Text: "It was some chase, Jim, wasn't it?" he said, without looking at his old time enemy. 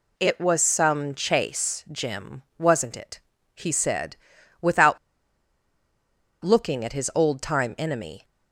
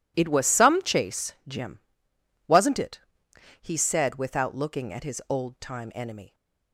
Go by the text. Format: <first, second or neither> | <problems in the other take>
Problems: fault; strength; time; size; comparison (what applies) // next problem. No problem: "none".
second | pauses between "without" and "looking"; strong; at 4.9 s; 1.4 s long